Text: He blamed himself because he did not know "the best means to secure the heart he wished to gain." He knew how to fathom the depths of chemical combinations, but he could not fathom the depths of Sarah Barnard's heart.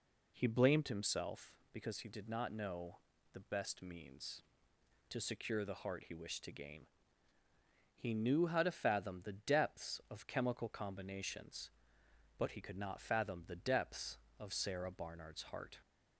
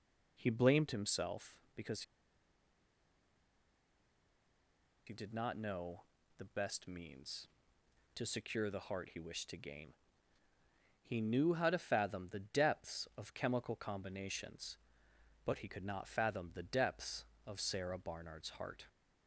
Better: first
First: pauses between "know" and "the"; slight; at 2.9 s; 0.32 s long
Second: pauses between "because" and "he"; strong; at 2.0 s; 3.0 s long // pauses between "know" and "the"; slight; at 6.0 s; 0.32 s long

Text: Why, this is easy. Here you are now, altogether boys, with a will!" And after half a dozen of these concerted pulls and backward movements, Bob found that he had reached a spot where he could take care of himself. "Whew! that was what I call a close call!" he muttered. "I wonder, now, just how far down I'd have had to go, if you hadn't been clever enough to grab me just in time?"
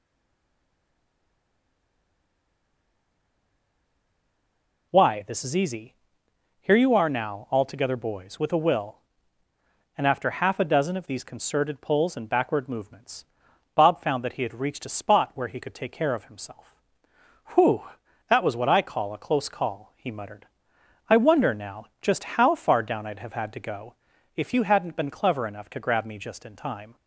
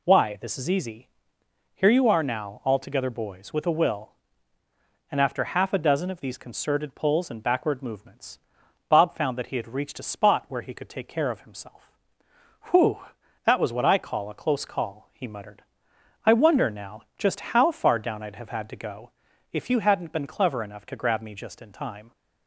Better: second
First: stays silent before the first word; strong; until 4.9 s; 4.9 s long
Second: none

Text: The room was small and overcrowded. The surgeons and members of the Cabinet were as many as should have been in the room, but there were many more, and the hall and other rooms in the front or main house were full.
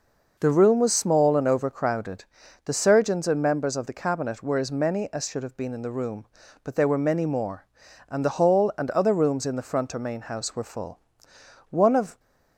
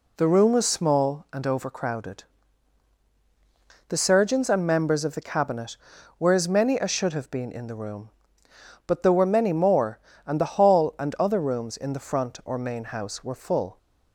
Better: second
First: goes on to say "One of"; slight; from 11.7 s on; 0.48 s long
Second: none

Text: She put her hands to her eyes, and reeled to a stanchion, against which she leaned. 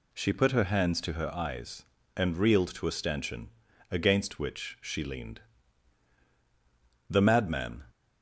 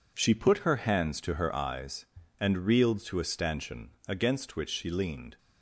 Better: second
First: goes on to say "The madman"; noticeable; from 7.0 s on; 0.74 s long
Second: none

